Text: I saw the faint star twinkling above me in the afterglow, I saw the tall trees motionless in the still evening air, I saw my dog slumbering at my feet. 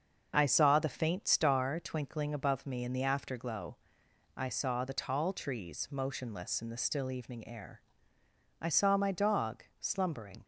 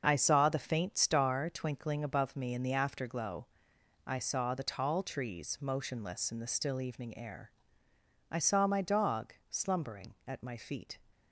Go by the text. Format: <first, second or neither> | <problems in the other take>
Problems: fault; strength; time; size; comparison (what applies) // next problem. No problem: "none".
second | starts louder than the rest; until 1.3 s; 6.5 dB; also in the second // pauses between "dog" and "slumbering"; slight; at 9.6 s; 0.16 s long; slight in the second // stops before "at my feet"; at 10.4 s